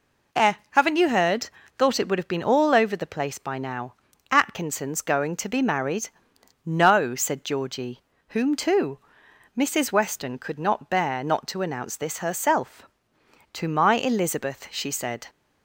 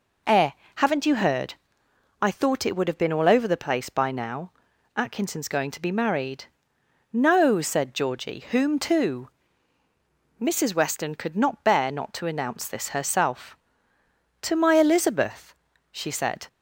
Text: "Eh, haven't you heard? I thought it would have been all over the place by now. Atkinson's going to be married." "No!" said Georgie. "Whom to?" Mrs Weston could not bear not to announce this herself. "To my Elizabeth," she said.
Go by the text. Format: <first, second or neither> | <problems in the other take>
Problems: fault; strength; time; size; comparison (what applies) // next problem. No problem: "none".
second | skips "I"; at 1.6 s